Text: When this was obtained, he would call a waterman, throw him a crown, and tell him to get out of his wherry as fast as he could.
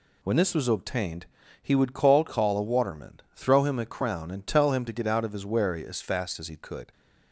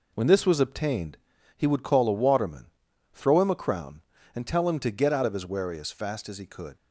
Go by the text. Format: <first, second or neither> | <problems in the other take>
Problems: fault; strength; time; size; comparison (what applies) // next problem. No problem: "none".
second | says "call" twice; at 2.2 s